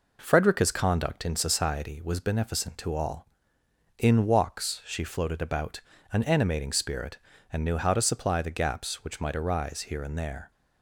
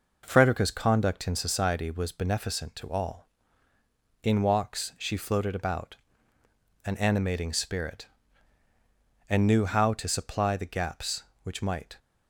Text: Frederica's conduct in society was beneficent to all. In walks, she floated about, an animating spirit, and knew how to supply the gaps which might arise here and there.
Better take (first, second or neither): first